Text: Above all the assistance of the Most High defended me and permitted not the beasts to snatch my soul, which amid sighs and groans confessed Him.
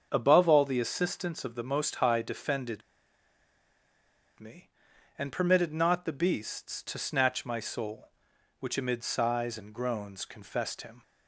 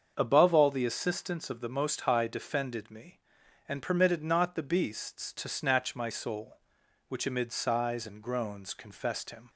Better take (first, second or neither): second